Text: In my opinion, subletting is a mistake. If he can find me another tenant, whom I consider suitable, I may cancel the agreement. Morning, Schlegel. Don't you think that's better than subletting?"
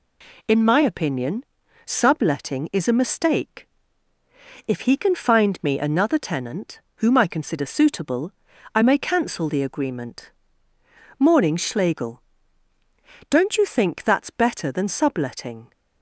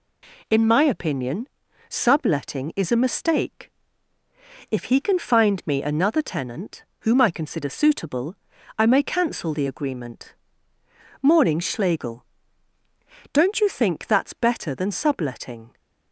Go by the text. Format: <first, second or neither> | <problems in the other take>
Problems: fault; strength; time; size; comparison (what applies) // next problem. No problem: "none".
neither | none